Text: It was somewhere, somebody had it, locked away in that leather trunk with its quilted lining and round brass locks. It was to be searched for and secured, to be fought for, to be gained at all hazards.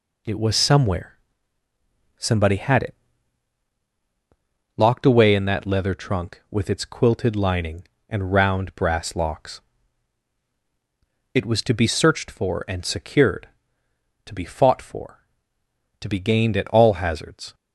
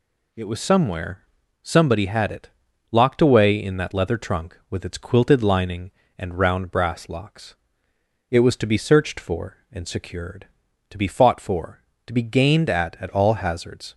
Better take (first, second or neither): first